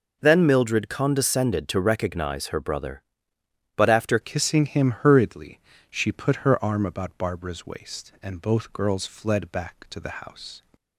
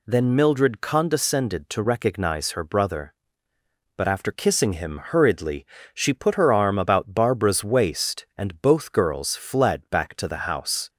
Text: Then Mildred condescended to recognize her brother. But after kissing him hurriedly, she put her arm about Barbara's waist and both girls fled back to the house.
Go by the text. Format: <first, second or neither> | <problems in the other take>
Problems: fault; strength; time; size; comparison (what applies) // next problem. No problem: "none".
second | changes voice at "kissing"; from 4.2 s on; 6.4 s long